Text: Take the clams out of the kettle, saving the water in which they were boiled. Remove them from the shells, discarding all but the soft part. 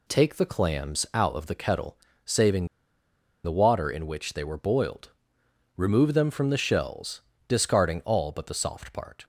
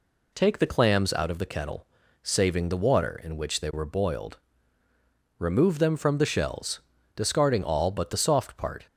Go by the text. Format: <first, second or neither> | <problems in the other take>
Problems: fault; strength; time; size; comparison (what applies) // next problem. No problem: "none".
second | pauses between "saving" and "the"; noticeable; at 2.6 s; 0.77 s long